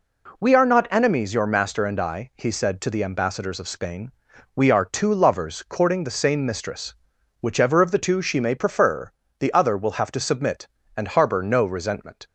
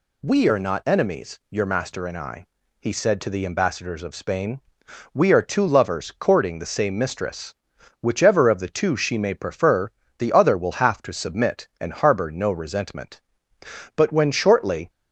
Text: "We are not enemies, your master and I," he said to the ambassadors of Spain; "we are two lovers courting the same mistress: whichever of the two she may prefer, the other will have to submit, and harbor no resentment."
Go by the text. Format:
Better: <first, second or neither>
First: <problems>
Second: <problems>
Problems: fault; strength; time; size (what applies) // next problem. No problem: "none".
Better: first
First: none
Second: goes on to say "But when shortly"; noticeable; from 13.9 s on; 0.94 s long